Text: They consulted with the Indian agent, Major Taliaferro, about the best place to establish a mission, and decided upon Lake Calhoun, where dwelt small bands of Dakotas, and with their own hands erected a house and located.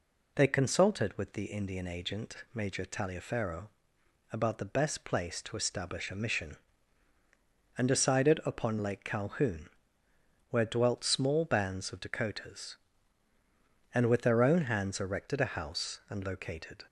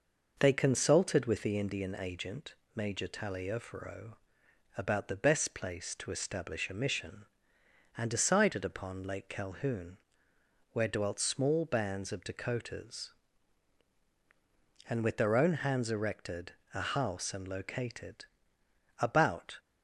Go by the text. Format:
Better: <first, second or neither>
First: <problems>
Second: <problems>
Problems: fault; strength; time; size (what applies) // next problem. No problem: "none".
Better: first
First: none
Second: pauses between "erected" and "a"; slight; at 16.5 s; 0.22 s long // goes on to say "About"; from 18.9 s on; 0.58 s long